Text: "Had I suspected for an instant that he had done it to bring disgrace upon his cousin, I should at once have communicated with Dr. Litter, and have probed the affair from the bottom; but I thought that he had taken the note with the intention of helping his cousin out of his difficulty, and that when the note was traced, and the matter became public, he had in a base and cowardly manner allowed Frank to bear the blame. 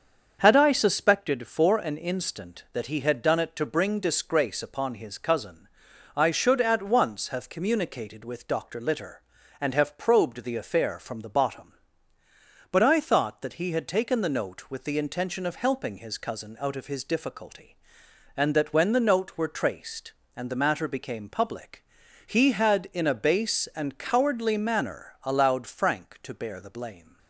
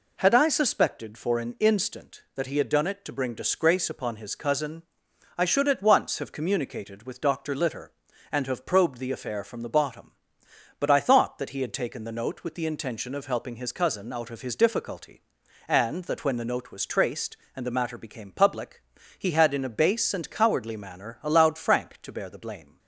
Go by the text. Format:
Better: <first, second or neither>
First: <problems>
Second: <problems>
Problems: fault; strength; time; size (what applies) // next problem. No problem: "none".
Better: second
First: starts louder than the rest; until 1.4 s; 7 dB // says "were" for "was"; at 19.3 s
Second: none